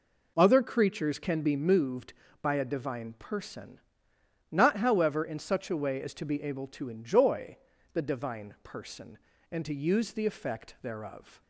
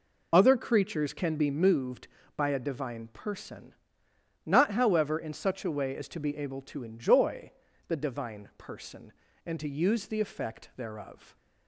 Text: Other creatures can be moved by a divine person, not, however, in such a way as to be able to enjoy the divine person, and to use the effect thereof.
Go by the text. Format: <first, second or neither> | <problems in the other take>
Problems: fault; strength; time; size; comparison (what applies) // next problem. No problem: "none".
first | loses the start of "Other"; at 0.3 s; 30 ms // pauses between "enjoy" and "the"; at 7.5 s; 0.38 s long; also in the first